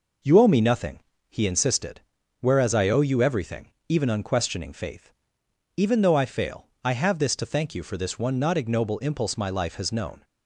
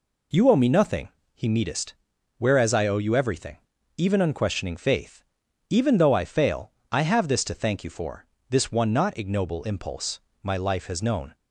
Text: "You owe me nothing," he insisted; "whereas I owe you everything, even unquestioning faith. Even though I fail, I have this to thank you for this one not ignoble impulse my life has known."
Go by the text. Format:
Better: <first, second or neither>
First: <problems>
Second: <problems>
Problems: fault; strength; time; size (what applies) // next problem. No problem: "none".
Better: first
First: none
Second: says "meetest" for "insisted"; at 1.4 s // pauses between "for" and "this"; slight; at 8.2 s; 0.22 s long // pauses between "impulse" and "my"; slight; at 10.2 s; 0.20 s long